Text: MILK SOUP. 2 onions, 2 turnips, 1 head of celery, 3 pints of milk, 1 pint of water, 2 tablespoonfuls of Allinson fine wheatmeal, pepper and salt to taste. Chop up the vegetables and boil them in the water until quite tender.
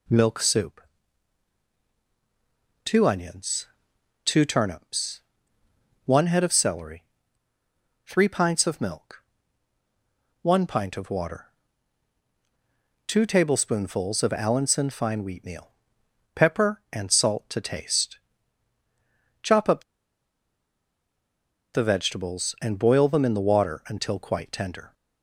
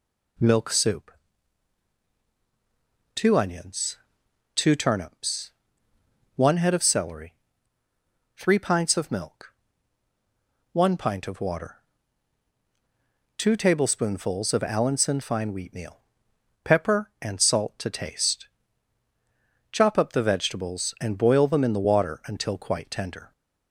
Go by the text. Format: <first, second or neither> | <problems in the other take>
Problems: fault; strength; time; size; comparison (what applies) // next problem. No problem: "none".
second | pauses between "up" and "the"; strong; at 19.8 s; 1.9 s long